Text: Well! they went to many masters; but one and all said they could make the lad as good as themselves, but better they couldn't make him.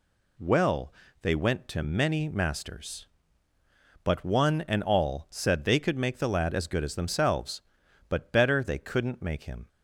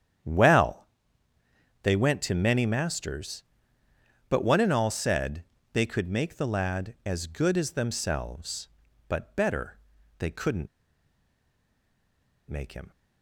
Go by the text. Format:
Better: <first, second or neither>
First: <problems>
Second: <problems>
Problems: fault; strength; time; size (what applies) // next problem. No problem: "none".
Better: first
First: none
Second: starts louder than the rest; strong; until 2.1 s; 9 dB // pauses between "said" and "they"; slight; at 5.4 s; 0.28 s long // pauses between "better" and "they"; at 9.7 s; 0.40 s long // pauses between "couldn't" and "make"; strong; at 10.6 s; 1.8 s long